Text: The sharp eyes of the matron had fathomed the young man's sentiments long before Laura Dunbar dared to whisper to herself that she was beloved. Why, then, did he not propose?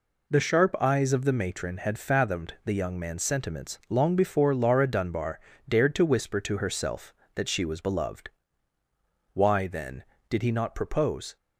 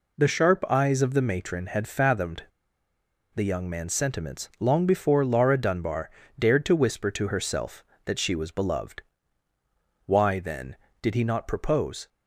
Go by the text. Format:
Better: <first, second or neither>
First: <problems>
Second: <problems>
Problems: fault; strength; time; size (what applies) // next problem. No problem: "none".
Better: first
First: pauses between "Dunbar" and "dared"; slight; at 5.3 s; 0.28 s long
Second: pauses between "fathomed" and "the"; noticeable; at 2.4 s; 0.91 s long // pauses between "Dunbar" and "dared"; slight; at 6.1 s; 0.28 s long